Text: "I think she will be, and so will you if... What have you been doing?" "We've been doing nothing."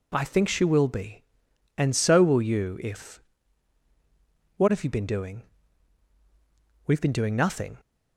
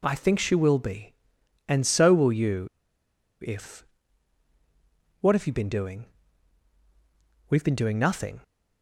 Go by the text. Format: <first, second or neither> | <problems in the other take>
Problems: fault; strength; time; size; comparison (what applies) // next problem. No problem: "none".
first | pauses between "you" and "if"; noticeable; at 2.6 s; 0.76 s long